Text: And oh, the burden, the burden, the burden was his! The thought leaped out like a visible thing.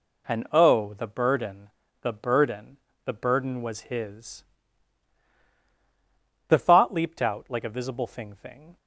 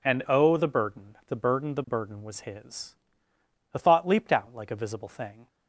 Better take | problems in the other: second | says "thing" twice; at 8.3 s

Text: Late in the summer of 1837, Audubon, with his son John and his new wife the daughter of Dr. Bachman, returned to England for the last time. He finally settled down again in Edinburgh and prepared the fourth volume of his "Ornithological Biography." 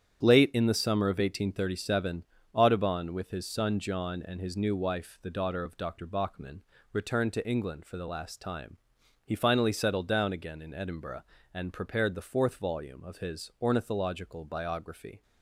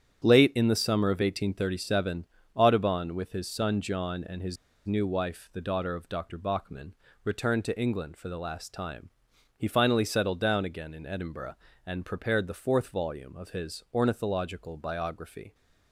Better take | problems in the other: first | starts louder than the rest; strong; until 1.2 s; 9 dB; strong in the first // pauses between "his" and "new"; slight; at 4.5 s; 0.30 s long

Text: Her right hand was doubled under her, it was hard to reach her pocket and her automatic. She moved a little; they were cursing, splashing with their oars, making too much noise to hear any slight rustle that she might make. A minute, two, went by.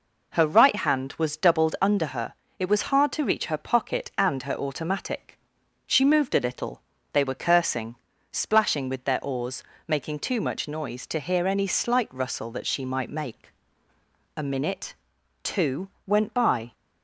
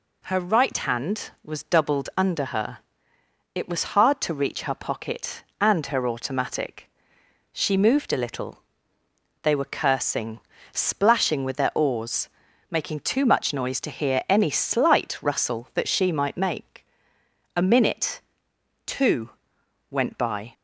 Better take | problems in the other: neither | none

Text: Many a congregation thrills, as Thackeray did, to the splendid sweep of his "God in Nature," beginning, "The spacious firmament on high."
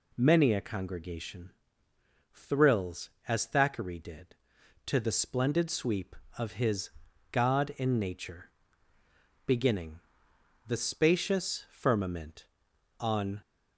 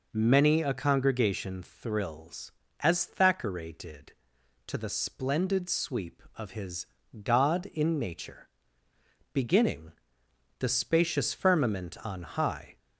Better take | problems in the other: second | pauses between "congregation" and "thrills"; noticeable; at 1.5 s; 0.84 s long // pauses between "his" and "God"; at 6.9 s; 0.40 s long; slight in the second // stops before "high"; at 13.4 s

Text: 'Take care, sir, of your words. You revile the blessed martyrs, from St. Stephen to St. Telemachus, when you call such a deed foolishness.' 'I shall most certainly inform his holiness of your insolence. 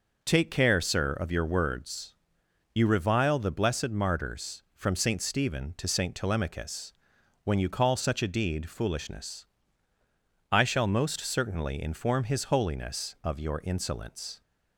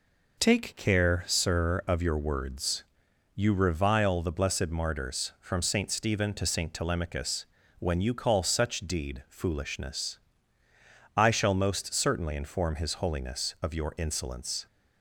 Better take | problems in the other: first | skips "a"; at 8.7 s

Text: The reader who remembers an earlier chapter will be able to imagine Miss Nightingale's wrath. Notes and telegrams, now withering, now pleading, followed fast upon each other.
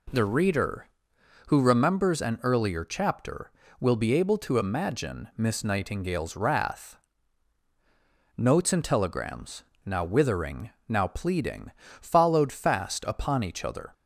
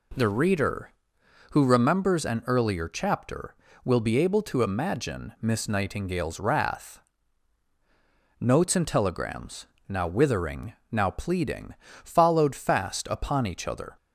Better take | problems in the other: neither | none

